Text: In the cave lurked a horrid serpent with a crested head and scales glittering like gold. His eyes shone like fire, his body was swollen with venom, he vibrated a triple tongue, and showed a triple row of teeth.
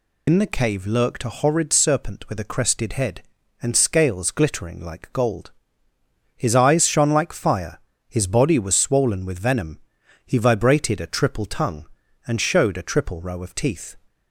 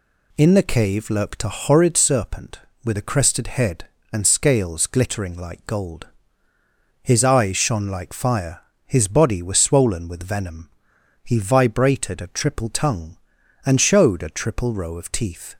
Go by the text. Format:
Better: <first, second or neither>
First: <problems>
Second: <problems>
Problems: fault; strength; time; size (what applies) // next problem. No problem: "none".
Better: second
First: loses the start of "In"; at 0.2 s; 100 ms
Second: none